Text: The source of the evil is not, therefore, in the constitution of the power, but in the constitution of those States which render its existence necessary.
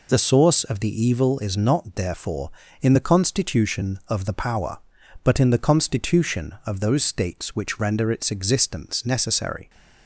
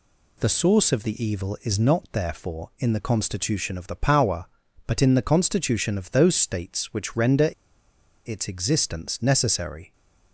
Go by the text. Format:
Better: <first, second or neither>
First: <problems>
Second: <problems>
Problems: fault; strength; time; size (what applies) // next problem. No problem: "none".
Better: first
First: none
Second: pauses between "render" and "its"; noticeable; at 7.5 s; 0.77 s long